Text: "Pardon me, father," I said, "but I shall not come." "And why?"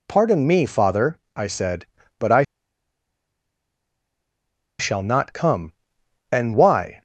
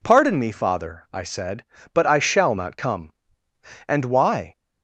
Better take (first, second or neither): second